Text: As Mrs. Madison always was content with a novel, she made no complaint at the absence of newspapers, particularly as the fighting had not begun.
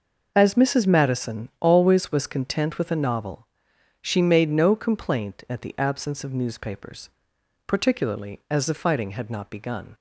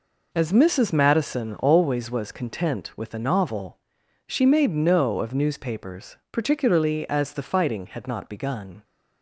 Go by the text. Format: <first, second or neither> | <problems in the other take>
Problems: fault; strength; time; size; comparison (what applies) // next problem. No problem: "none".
first | skips "complaint at the absence"; at 5.1 s